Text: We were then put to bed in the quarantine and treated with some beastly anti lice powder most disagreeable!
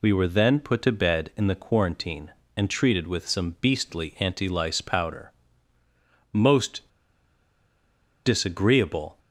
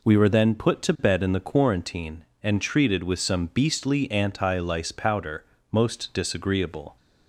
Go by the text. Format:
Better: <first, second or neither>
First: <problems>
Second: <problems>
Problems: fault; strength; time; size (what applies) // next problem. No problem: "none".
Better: second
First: pauses between "powder" and "most"; at 5.3 s; 1.0 s long // pauses between "most" and "disagreeable"; strong; at 6.8 s; 1.3 s long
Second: pauses between "powder" and "most"; slight; at 5.4 s; 0.28 s long